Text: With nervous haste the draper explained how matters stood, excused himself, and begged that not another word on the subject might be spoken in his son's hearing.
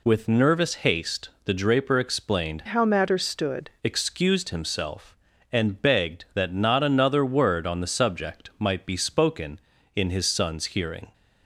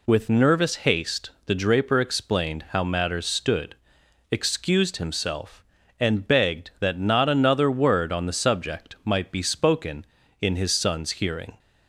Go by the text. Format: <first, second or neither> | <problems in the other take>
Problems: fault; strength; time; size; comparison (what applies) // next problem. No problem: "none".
second | pauses between "haste" and "the"; slight; at 1.2 s; 0.16 s long; slight in the second // changes voice from "how" to "stood"; from 2.6 to 3.7 s; 1.1 s long